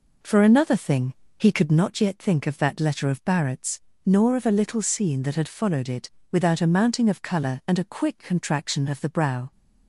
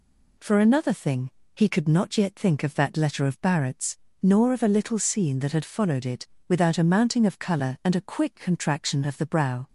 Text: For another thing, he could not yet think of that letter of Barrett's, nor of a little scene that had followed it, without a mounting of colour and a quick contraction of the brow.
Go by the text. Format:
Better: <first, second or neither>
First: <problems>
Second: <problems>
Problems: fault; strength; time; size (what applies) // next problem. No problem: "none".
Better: second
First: starts louder than the rest; noticeable; until 1.9 s; 4.5 dB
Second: none